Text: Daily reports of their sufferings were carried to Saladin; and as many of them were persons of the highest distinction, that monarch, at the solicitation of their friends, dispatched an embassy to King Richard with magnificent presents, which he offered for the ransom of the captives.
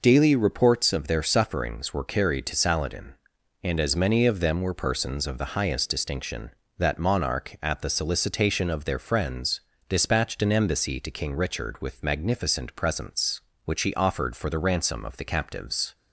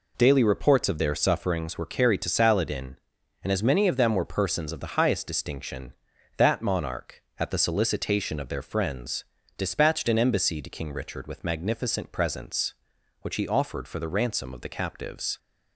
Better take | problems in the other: neither | none

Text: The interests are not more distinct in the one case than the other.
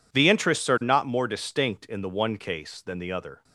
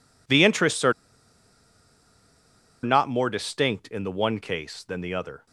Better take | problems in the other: first | pauses between "are" and "not"; strong; at 0.9 s; 1.9 s long

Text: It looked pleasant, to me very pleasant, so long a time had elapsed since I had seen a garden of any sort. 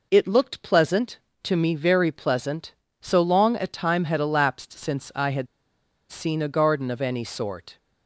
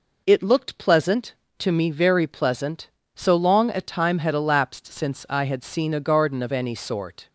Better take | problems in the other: second | pauses between "had" and "seen"; noticeable; at 5.4 s; 0.64 s long

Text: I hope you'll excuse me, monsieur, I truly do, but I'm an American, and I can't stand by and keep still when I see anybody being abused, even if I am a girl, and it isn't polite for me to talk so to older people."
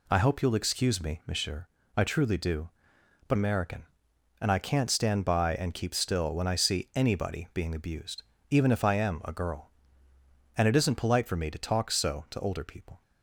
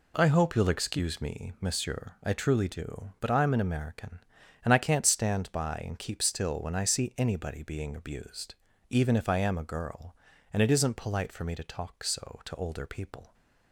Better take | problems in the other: second | skips "I'm an"; at 3.3 s

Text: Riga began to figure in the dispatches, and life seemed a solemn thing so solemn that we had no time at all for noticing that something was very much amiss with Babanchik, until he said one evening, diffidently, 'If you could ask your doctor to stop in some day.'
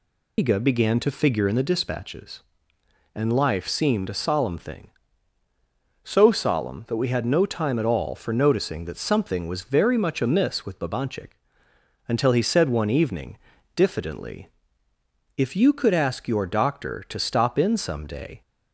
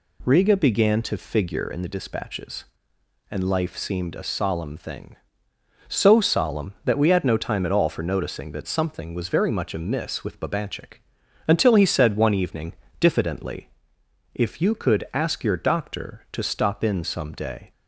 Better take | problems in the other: second | loses the start of "Riga"; at 0.3 s; 150 ms

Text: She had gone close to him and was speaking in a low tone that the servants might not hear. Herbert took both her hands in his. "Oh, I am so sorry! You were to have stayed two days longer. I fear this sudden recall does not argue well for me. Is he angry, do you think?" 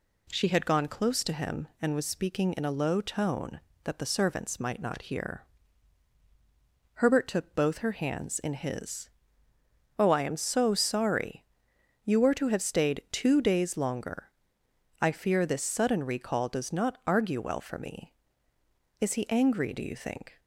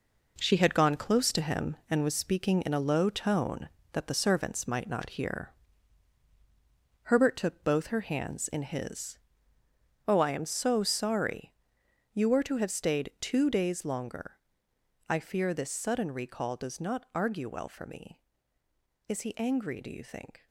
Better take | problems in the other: first | gets quieter; strong; throughout; 9 dB

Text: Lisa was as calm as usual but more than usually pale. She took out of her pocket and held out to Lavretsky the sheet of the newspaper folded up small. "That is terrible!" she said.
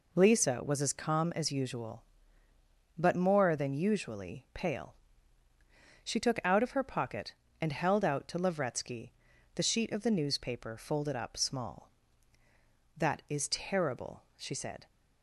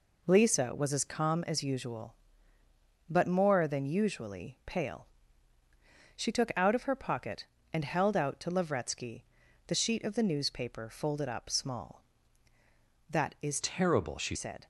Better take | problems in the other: first | pauses between "Lavretsky" and "the"; at 9.2 s; 0.42 s long; also in the first // changes voice from "terrible" to "she"; from 13.6 to 14.3 s; 0.7 s long

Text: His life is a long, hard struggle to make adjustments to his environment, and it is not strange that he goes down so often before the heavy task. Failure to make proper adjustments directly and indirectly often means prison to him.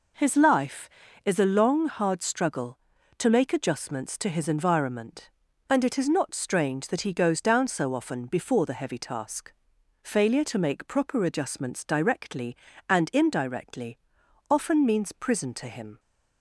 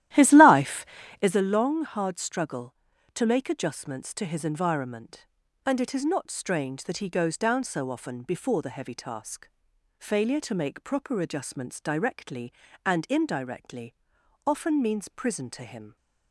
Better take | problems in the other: first | starts louder than the rest; strong; until 1.4 s; 13.5 dB // pauses between "indirectly" and "often"; noticeable; at 13.9 s; 0.52 s long; noticeable in the first

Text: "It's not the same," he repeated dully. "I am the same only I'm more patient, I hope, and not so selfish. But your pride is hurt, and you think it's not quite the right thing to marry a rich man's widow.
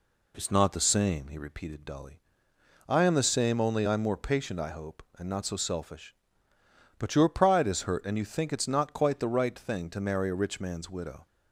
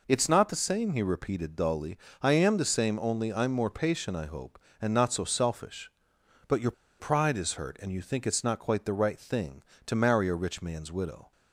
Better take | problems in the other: first | pauses between "your" and "pride"; slight; at 6.7 s; 0.27 s long

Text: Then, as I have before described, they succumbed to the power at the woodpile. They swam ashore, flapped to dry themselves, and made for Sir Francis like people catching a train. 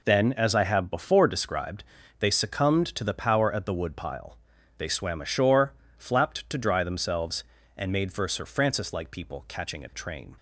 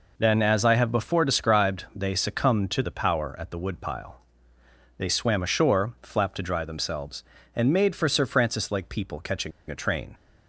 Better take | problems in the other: first | pauses between "catching" and "a"; slight; at 9.5 s; 0.19 s long

